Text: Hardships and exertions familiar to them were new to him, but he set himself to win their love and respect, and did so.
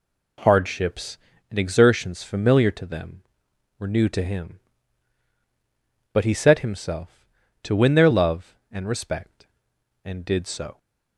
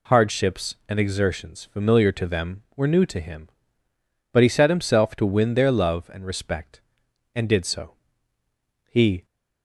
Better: first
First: none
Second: goes on to say "He"; slight; from 8.8 s on; 0.38 s long

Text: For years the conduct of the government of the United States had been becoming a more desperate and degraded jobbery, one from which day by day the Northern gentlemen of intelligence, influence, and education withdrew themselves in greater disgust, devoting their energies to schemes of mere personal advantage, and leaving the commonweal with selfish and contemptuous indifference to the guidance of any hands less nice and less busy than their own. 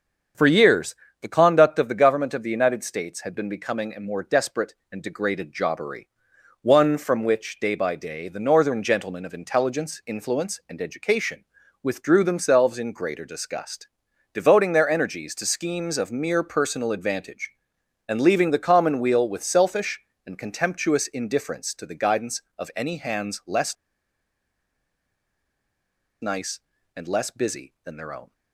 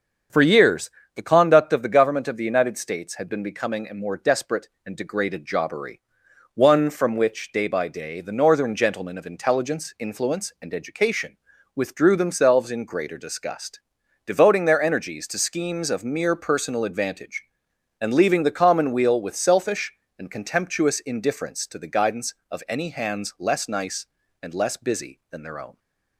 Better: second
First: starts louder than the rest; strong; until 1.6 s; 7.5 dB // pauses between "years" and "the"; slight; at 0.9 s; 0.28 s long // pauses between "education" and "withdrew"; slight; at 11.4 s; 0.36 s long // pauses between "less" and "nice"; strong; at 23.7 s; 2.4 s long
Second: starts louder than the rest; strong; until 1.5 s; 7.5 dB // pauses between "years" and "the"; slight; at 0.8 s; 0.26 s long // pauses between "education" and "withdrew"; slight; at 11.3 s; 0.36 s long

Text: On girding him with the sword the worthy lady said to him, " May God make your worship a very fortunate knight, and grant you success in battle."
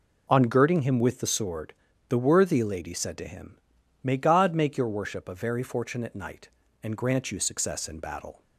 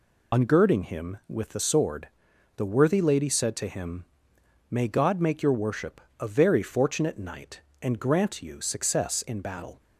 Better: first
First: pauses between "sword" and "the"; slight; at 1.7 s; 0.36 s long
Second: loses the start of "On"; at 0.3 s; 60 ms // pauses between "sword" and "the"; noticeable; at 2.0 s; 0.48 s long // pauses between "worship" and "a"; slight; at 6.0 s; 0.20 s long

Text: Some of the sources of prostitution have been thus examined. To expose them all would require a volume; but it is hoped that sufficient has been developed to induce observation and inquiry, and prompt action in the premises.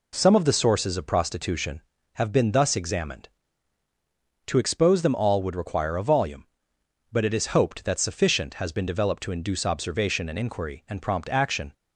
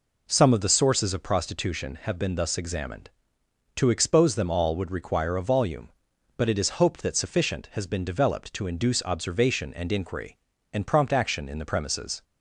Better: second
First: stops before "in the premises"; at 11.7 s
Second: none

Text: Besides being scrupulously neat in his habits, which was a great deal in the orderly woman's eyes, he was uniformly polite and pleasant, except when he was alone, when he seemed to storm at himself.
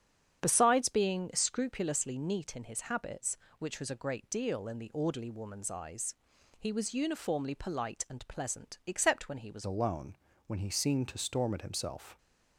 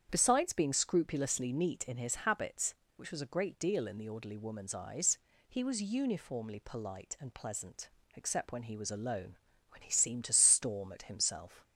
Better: second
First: starts louder than the rest; strong; until 1.4 s; 8.5 dB // changes voice at "alone"; from 9.6 s on; 2.5 s long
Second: starts louder than the rest; strong; until 1.1 s; 8.5 dB

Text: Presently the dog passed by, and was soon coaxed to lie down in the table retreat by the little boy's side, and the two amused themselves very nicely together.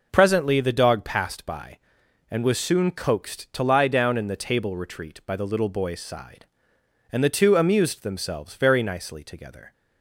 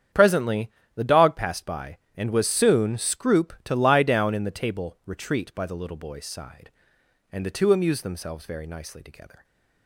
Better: first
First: none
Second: starts louder than the rest; strong; until 1.3 s; 8.5 dB // pauses between "Presently" and "the"; slight; at 0.7 s; 0.24 s long // says "scroop" for "coaxed"; at 2.9 s // stays silent after the last word; slight; from 9.3 s on; 0.5 s long

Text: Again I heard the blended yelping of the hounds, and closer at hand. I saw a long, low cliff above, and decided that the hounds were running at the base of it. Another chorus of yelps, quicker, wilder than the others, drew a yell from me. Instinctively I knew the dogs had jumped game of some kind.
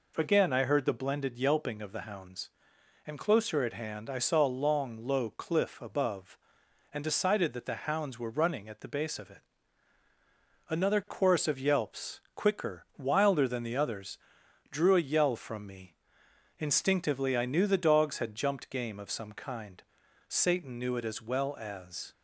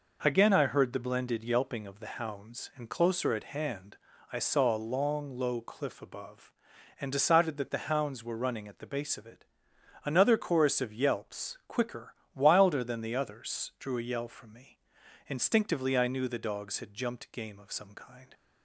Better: second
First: goes on to say "Satan knew it as well as"; strong; from 20.2 s on; 1.8 s long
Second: none

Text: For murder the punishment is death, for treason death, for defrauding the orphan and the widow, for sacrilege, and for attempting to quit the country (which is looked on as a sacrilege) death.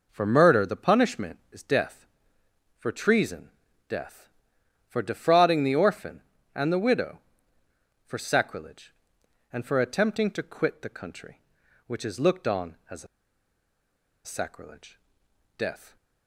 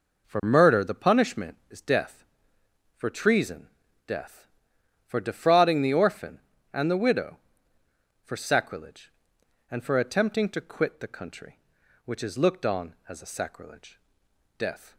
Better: second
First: pauses between "treason" and "death"; at 3.4 s; 0.40 s long // pauses between "a" and "sacrilege"; at 13.0 s; 1.1 s long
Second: pauses between "treason" and "death"; at 3.6 s; 0.40 s long

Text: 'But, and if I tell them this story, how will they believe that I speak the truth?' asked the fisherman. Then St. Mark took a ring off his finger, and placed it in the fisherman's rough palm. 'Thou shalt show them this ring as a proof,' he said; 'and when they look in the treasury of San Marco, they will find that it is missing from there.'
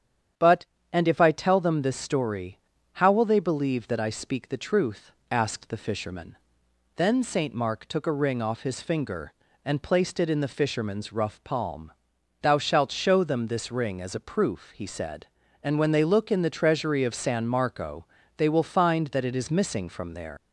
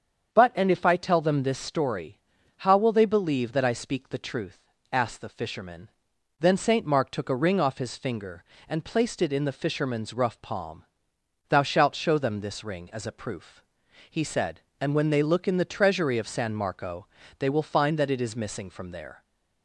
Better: second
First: starts louder than the rest; strong; until 1.6 s; 9 dB // leaves "there" unfinished; at 20.3 s; 130 ms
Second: starts louder than the rest; strong; until 1.4 s; 7.5 dB

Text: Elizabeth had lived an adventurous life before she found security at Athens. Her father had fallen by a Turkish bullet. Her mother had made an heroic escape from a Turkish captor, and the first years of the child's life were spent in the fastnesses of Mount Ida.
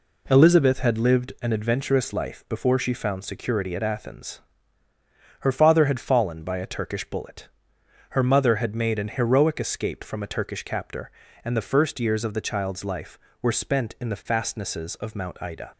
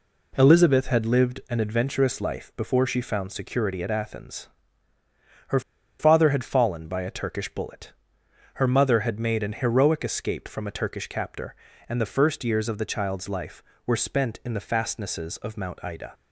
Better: first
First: none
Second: pauses between "Her" and "father"; at 5.5 s; 0.39 s long

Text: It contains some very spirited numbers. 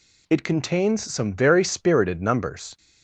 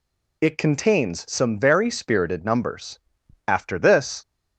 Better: first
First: none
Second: goes on to say "After this"; noticeable; from 3.4 s on; 0.74 s long

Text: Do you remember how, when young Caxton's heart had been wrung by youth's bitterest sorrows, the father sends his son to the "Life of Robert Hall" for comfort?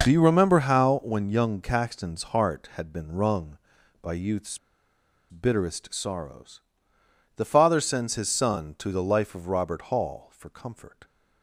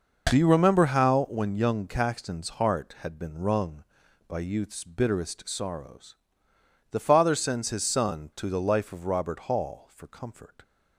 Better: second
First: pauses between "youth's" and "bitterest"; noticeable; at 4.5 s; 0.72 s long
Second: none

